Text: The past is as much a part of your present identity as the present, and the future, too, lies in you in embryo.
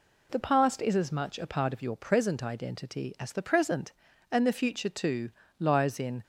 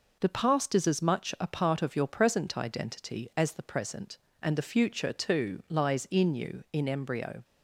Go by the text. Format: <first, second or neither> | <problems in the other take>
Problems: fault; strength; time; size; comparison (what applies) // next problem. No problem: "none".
second | stops before "you in embryo"; at 6.2 s